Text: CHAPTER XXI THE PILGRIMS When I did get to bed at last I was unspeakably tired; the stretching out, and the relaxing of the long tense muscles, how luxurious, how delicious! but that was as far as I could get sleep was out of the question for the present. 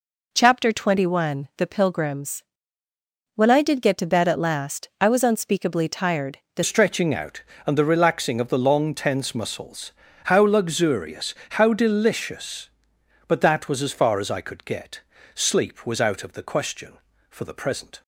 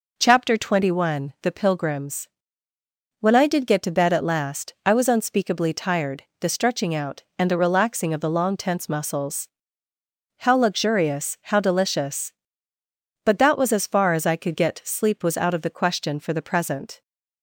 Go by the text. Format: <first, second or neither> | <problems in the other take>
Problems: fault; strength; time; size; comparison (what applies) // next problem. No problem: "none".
second | pauses between "PILGRIMS" and "When"; noticeable; at 2.4 s; 0.92 s long; noticeable in the second // changes voice at "stretching"; from 6.6 s on; 11.4 s long // pauses between "get" and "sleep"; slight; at 15.0 s; 0.34 s long